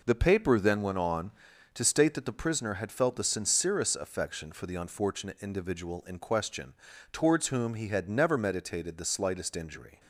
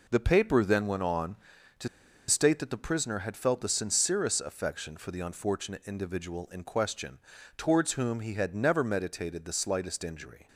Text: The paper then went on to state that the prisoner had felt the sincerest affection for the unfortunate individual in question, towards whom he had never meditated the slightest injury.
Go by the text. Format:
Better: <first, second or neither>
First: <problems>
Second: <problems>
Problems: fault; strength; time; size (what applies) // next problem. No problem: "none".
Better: first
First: none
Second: pauses between "to" and "state"; at 1.8 s; 0.41 s long